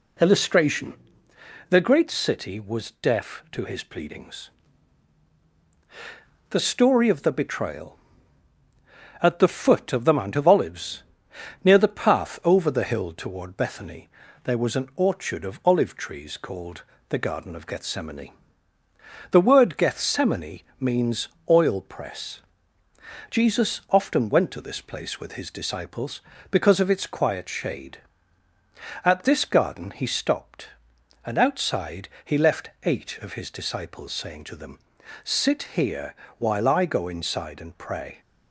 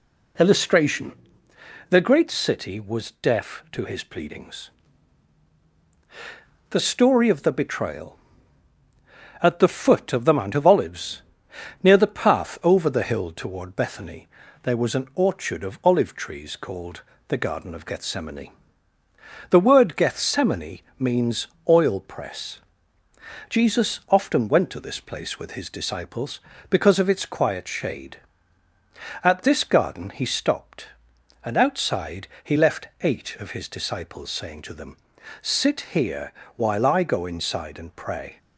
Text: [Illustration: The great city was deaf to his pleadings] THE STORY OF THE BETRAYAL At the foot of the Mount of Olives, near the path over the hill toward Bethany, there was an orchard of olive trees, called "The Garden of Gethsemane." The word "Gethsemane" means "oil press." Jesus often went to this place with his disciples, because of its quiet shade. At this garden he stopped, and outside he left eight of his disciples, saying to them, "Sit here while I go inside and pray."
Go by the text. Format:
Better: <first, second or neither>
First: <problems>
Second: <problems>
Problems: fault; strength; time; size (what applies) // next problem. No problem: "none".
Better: neither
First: pauses between "pleadings" and "THE"; strong; at 4.4 s; 2.0 s long // pauses between "called" and "The"; slight; at 16.8 s; 0.26 s long // pauses between "Gethsemane" and "means"; slight; at 20.6 s; 0.18 s long // pauses between "means" and "oil"; slight; at 21.2 s; 0.22 s long // pauses between "outside" and "he"; slight; at 32.1 s; 0.16 s long // pauses between "here" and "while"; slight; at 36.1 s; 0.24 s long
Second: pauses between "pleadings" and "THE"; strong; at 4.6 s; 2.0 s long // pauses between "called" and "The"; slight; at 17.0 s; 0.26 s long // pauses between "Gethsemane" and "means"; slight; at 20.8 s; 0.18 s long // pauses between "means" and "oil"; slight; at 21.4 s; 0.22 s long // pauses between "outside" and "he"; slight; at 32.2 s; 0.16 s long // pauses between "here" and "while"; slight; at 36.3 s; 0.24 s long